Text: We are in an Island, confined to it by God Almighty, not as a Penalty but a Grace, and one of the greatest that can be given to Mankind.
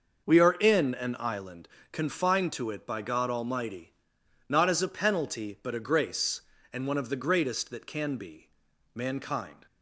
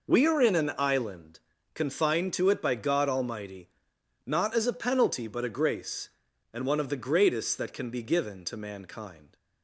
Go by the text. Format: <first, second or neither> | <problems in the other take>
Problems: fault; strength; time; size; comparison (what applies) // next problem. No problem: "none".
second | skips "given to"; at 8.7 s